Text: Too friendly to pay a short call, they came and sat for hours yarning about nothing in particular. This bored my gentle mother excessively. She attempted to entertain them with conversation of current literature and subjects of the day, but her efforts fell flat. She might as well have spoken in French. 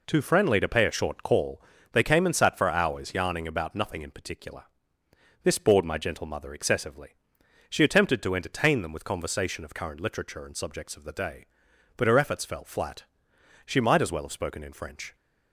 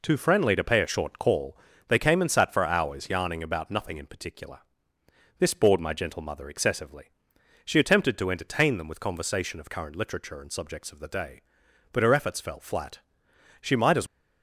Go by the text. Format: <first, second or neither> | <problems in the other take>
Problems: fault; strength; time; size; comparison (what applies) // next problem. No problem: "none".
first | stops before "well have spoken in French"; at 14.0 s